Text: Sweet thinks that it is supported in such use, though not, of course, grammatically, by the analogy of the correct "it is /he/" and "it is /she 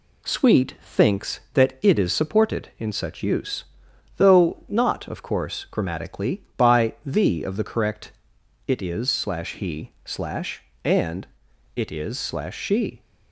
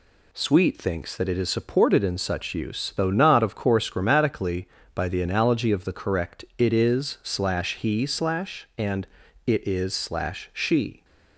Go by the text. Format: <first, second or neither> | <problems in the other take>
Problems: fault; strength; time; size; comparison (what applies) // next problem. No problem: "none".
second | skips "analogy"; at 7.4 s // pauses between "correct" and "it"; noticeable; at 8.1 s; 0.54 s long // pauses between "and" and "it"; noticeable; at 11.2 s; 0.48 s long; also in the second